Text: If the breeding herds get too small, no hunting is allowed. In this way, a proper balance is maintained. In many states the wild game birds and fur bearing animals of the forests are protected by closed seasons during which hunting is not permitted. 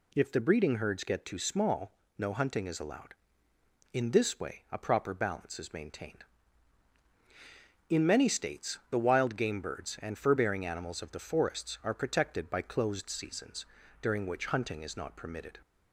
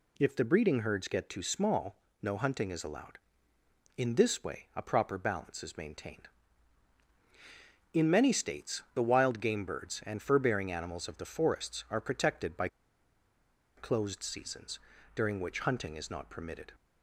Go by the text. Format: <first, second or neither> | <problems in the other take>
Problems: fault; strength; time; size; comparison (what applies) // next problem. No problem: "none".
first | pauses between "by" and "closed"; at 12.6 s; 1.0 s long // pauses between "seasons" and "during"; slight; at 14.7 s; 0.36 s long; slight in the first